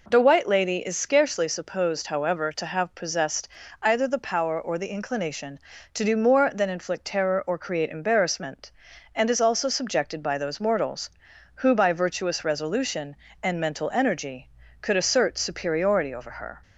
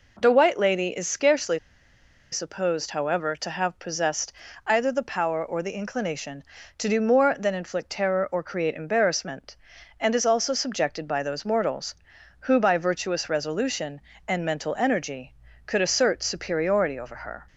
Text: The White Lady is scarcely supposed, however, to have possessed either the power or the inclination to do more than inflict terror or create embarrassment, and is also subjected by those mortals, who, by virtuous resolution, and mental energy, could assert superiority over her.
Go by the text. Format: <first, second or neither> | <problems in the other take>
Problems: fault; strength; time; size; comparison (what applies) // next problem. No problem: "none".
first | pauses between "scarcely" and "supposed"; noticeable; at 1.5 s; 0.73 s long // pauses between "possessed" and "either"; slight; at 4.3 s; 0.34 s long; slight in the first